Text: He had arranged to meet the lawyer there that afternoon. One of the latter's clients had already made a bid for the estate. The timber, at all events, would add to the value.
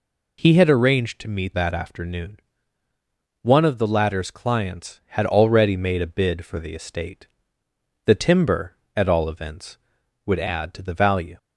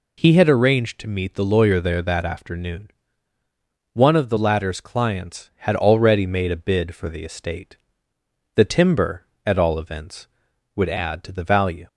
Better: second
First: skips "the lawyer there"; at 1.5 s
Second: none

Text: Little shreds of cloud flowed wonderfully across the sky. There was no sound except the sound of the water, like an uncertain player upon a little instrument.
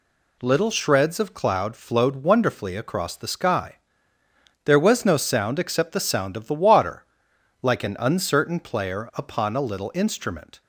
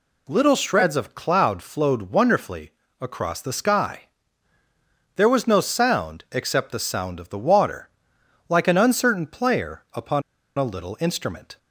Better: first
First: none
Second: pauses between "wonderfully" and "across"; slight; at 2.7 s; 0.30 s long // pauses between "upon" and "a"; slight; at 10.2 s; 0.35 s long

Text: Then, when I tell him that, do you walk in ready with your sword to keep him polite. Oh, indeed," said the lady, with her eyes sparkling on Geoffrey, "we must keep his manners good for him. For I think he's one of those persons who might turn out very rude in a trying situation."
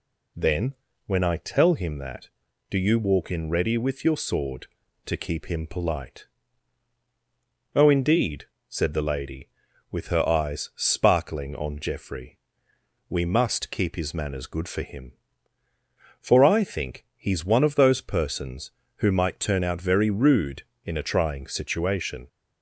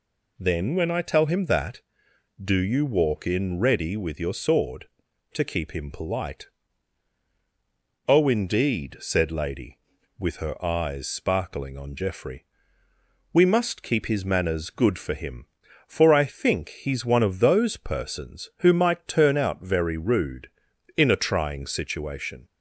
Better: first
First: none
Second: skips "the"; at 9.3 s

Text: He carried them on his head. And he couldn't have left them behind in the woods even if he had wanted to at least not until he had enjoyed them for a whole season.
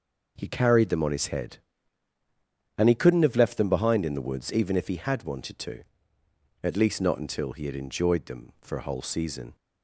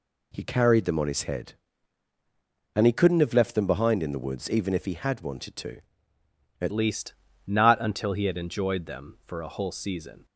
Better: first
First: none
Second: changes voice at "least"; from 6.7 s on; 3.5 s long // pauses between "least" and "not"; slight; at 7.1 s; 0.34 s long

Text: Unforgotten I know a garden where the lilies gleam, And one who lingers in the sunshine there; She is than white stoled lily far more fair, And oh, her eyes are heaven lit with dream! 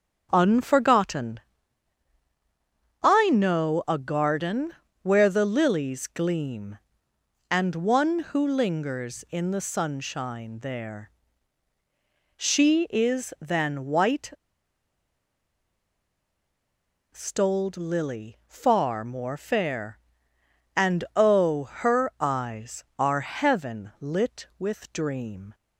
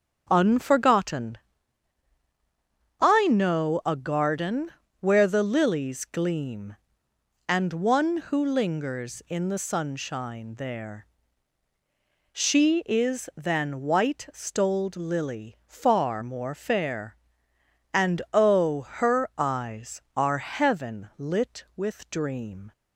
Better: second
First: starts louder than the rest; strong; until 1.3 s; 7.5 dB // pauses between "Unforgotten" and "I"; strong; at 1.3 s; 1.6 s long // pauses between "garden" and "where"; slight; at 4.7 s; 0.28 s long // pauses between "white" and "stoled"; strong; at 14.2 s; 2.8 s long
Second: starts louder than the rest; strong; until 1.3 s; 7.5 dB // pauses between "Unforgotten" and "I"; strong; at 1.3 s; 1.6 s long // pauses between "garden" and "where"; slight; at 4.7 s; 0.28 s long

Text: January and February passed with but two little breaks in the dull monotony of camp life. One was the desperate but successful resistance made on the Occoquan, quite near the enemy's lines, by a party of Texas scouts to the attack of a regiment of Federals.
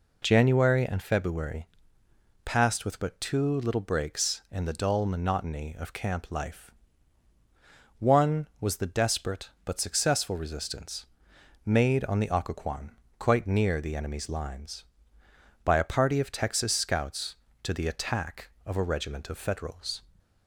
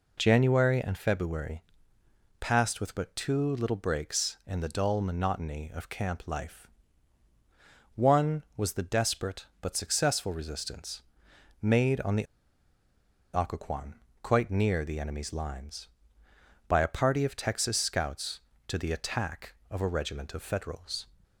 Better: first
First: pauses between "February" and "passed"; noticeable; at 1.6 s; 0.78 s long // pauses between "resistance" and "made"; noticeable; at 11.0 s; 0.60 s long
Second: pauses between "February" and "passed"; noticeable; at 1.6 s; 0.78 s long // pauses between "resistance" and "made"; noticeable; at 11.0 s; 0.60 s long // pauses between "the" and "Occoquan"; at 12.2 s; 1.0 s long

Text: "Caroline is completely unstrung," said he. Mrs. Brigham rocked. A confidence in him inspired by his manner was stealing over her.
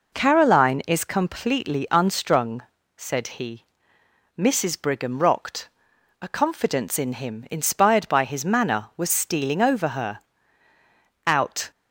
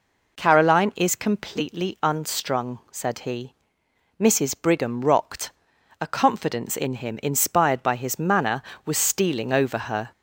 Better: second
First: goes on to say "Out"; slight; from 11.2 s on; 0.44 s long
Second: none

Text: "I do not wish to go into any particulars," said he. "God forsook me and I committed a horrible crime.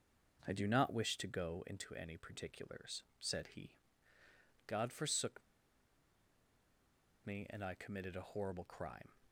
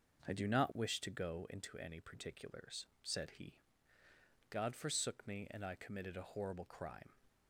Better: second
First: pauses between "forsook" and "me"; strong; at 5.4 s; 1.8 s long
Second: none

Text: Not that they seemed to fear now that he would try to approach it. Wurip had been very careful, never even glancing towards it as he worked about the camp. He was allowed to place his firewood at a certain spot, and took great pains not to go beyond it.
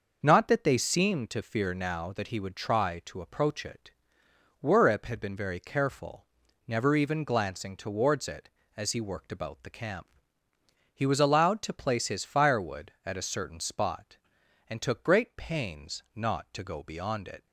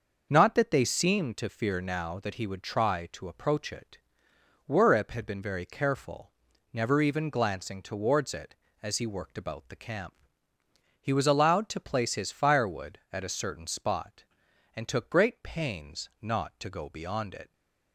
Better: neither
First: starts louder than the rest; noticeable; until 1.2 s; 6 dB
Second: starts louder than the rest; noticeable; until 1.3 s; 6 dB

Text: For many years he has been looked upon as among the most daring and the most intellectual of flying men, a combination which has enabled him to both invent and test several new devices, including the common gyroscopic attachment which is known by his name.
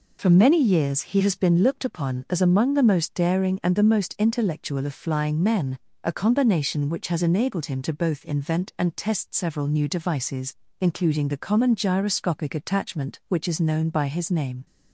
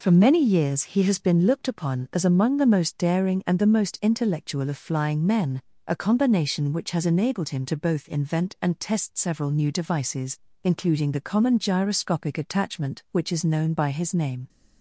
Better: neither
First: none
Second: none

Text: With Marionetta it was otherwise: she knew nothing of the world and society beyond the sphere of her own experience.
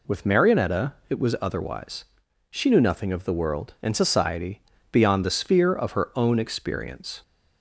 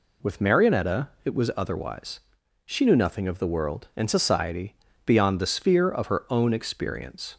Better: neither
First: pauses between "Marionetta" and "it"; slight; at 0.9 s; 0.16 s long // pauses between "society" and "beyond"; slight; at 4.6 s; 0.30 s long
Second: pauses between "Marionetta" and "it"; slight; at 1.0 s; 0.16 s long // pauses between "society" and "beyond"; slight; at 4.7 s; 0.30 s long

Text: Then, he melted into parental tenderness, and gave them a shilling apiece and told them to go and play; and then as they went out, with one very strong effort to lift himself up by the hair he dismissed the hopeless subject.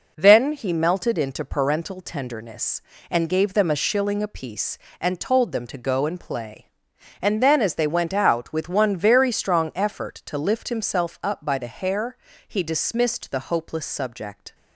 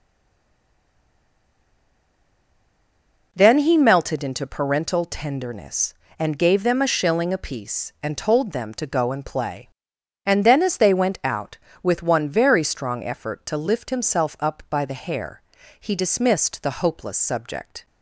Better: first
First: pauses between "hair" and "he"; slight; at 12.1 s; 0.30 s long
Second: stays silent before the first word; strong; until 3.3 s; 3.3 s long // pauses between "hair" and "he"; at 15.4 s; 0.38 s long

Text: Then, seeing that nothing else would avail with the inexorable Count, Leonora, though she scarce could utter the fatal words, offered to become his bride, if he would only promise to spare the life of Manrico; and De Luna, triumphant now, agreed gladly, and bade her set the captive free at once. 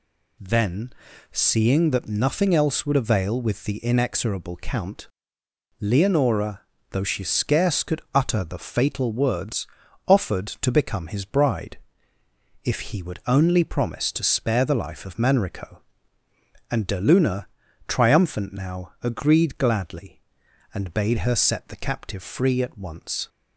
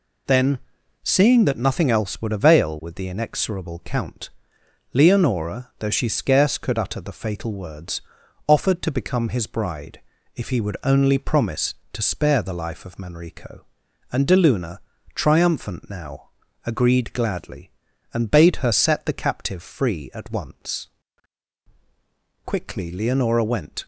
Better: first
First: none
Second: goes on to say "Quickly Leonora went"; from 22.4 s on; 1.4 s long

